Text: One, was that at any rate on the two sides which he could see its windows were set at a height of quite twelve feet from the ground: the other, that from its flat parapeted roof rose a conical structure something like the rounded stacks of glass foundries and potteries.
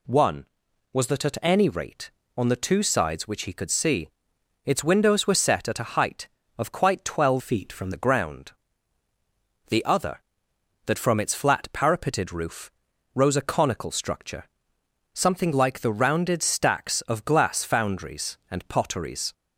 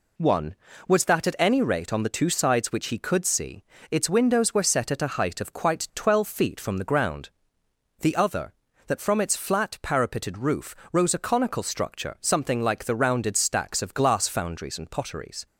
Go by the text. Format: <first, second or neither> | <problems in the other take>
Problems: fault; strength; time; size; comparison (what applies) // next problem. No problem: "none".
second | pauses between "see" and "its"; noticeable; at 4.0 s; 0.56 s long; slight in the second // changes voice from "feet" to "from"; from 7.3 to 7.9 s; 0.6 s long // pauses between "roof" and "rose"; at 12.7 s; 0.44 s long; slight in the second // pauses between "structure" and "something"; noticeable; at 14.4 s; 0.68 s long